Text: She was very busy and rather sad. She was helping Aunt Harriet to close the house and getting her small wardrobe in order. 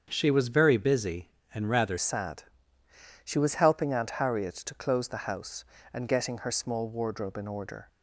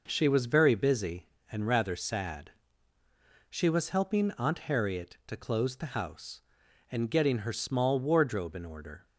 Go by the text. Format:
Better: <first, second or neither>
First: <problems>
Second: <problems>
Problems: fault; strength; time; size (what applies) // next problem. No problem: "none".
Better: second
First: starts louder than the rest; until 1.1 s; 7 dB // changes voice at "sad"; from 1.9 s on; 5.9 s long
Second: none